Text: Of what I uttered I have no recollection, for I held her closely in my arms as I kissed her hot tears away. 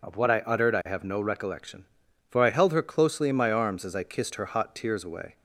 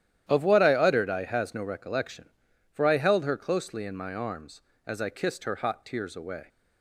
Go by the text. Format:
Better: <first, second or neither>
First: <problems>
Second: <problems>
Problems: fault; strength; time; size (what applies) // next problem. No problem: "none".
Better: first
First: none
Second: starts louder than the rest; strong; until 1.3 s; 11.5 dB // says "has" for "have"; at 1.2 s